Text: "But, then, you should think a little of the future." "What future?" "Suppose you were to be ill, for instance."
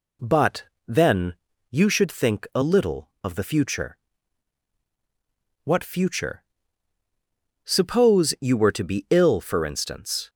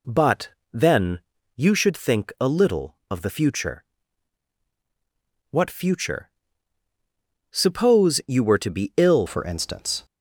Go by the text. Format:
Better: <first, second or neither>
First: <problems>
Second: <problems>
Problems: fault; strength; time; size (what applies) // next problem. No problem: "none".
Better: first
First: none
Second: changes voice at "for"; from 9.2 s on; 0.8 s long